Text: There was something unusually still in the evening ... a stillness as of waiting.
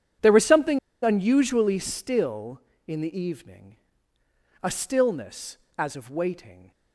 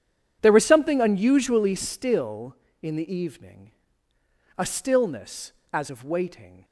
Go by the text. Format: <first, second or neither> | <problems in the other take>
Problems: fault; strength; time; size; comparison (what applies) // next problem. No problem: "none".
second | pauses between "something" and "unusually"; slight; at 0.7 s; 0.25 s long